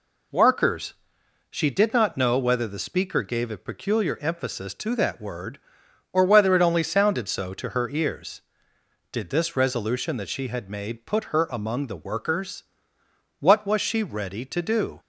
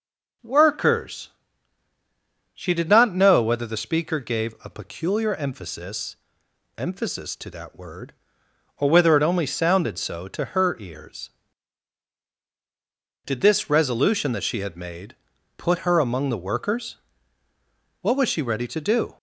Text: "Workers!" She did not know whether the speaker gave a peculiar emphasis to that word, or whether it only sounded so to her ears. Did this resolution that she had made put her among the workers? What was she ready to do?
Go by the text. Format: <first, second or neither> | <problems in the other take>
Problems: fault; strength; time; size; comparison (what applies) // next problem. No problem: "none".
first | says "emphasis" twice; at 6.7 s // pauses between "made" and "put"; at 15.1 s; 0.40 s long